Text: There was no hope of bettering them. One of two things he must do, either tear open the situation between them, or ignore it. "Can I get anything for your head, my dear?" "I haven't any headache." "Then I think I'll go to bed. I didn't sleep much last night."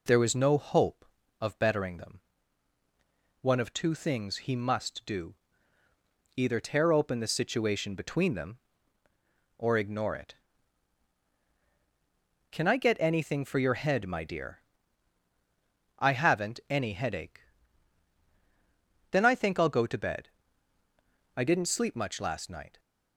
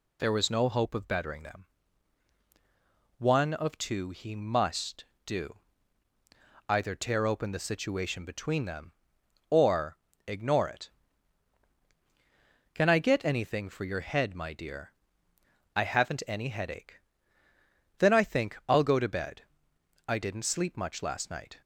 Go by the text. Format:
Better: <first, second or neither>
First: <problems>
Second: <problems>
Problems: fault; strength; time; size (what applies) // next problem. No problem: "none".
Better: first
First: none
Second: skips "things"; at 4.1 s // pauses between "or" and "ignore"; slight; at 9.9 s; 0.30 s long